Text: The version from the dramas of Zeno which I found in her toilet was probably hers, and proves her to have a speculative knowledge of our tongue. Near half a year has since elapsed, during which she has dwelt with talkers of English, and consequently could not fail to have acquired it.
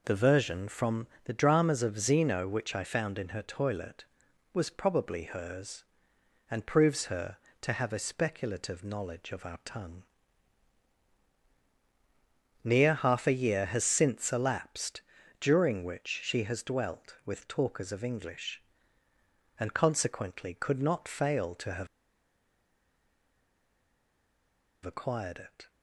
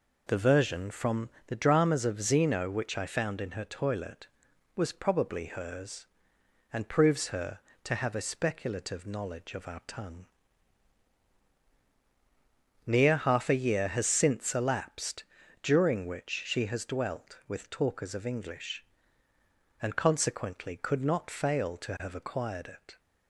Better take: second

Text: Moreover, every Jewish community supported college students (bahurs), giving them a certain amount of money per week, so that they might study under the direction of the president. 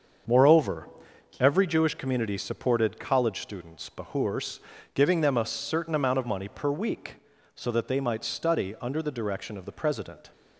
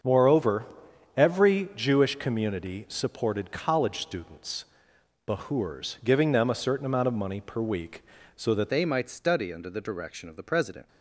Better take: first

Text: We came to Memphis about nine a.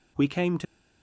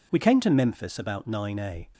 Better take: second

